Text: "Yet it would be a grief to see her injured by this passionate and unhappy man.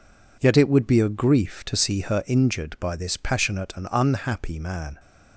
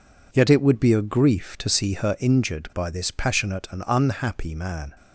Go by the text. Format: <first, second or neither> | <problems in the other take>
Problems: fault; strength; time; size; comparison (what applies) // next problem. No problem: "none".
neither | none